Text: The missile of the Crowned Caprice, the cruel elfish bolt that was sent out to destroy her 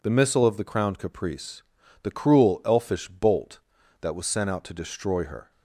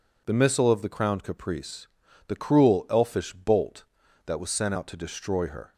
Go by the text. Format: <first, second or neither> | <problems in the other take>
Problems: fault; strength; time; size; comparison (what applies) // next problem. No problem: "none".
neither | none